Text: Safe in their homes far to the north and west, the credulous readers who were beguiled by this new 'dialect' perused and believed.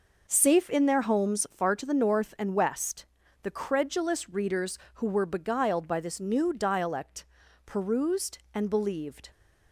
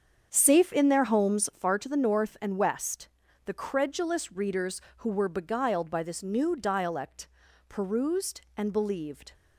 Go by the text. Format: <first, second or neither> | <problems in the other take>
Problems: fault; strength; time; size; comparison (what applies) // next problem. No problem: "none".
first | starts louder than the rest; strong; until 1.7 s; 7.5 dB // pauses between "dialect" and "perused"; at 7.2 s; 0.42 s long; also in the first